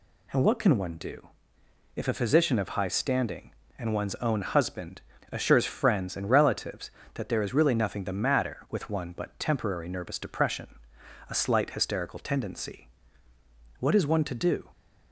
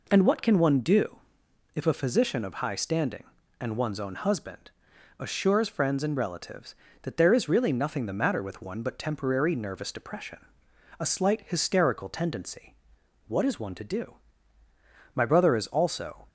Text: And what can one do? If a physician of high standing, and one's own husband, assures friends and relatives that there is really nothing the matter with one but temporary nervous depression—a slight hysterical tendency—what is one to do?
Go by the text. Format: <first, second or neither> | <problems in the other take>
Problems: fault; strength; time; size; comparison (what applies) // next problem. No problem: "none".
first | goes on to say "My brother is also"; noticeable; from 15.1 s on; 1.1 s long